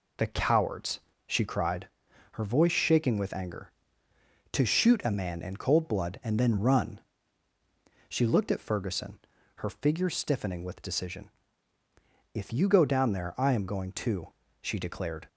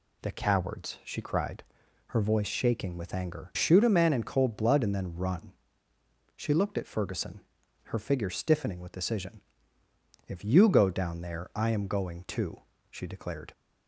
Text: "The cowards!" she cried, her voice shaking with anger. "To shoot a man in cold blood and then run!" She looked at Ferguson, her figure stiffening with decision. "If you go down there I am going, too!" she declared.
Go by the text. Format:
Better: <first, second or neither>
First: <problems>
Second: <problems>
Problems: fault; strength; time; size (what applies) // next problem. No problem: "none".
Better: first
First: none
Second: skips "To"; at 3.5 s